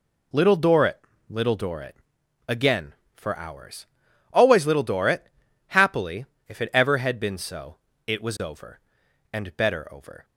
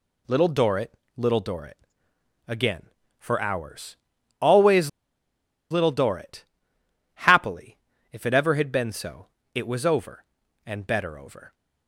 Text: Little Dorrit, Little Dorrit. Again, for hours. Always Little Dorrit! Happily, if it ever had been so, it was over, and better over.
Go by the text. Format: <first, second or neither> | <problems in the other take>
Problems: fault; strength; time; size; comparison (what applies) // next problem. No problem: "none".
first | pauses between "Always" and "Little"; noticeable; at 4.8 s; 0.81 s long